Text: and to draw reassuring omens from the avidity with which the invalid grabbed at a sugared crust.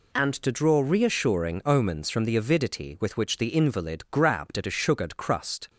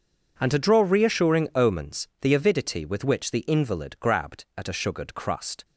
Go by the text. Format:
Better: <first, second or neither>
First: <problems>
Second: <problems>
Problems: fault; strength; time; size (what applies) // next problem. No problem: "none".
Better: first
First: none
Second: skips "from"; at 2.1 s